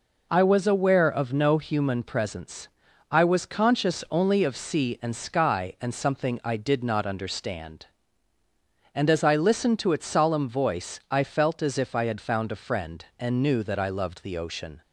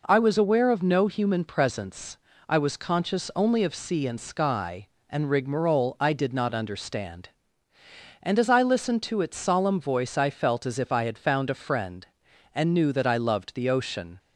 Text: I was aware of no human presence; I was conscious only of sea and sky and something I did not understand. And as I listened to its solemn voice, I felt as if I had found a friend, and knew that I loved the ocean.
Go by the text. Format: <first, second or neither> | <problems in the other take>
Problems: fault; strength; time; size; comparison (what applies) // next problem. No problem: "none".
first | says "rigmarole" for "something"; at 5.3 s